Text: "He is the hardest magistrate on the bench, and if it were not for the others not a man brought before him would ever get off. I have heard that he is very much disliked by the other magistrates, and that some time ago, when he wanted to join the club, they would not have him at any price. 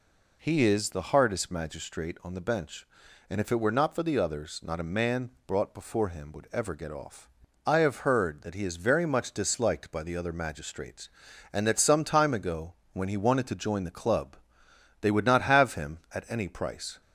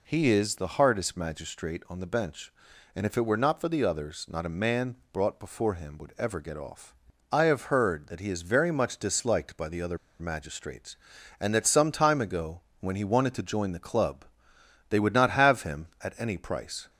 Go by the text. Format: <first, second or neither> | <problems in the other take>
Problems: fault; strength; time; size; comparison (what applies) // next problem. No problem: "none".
first | pauses between "man" and "brought"; slight; at 4.9 s; 0.18 s long; slight in the first // pauses between "other" and "magistrates"; slight; at 9.9 s; 0.21 s long